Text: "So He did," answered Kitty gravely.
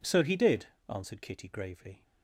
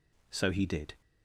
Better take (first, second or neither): first